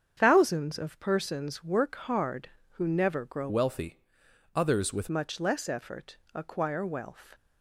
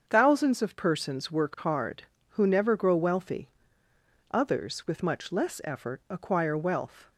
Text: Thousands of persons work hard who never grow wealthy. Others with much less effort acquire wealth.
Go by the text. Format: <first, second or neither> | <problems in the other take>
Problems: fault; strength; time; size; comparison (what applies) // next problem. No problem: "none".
second | starts louder than the rest; strong; until 1.1 s; 7.5 dB; strong in the second // changes voice from "wealthy" to "with"; from 3.4 to 5.0 s; 1.6 s long // pauses between "effort" and "acquire"; slight; at 6.1 s; 0.18 s long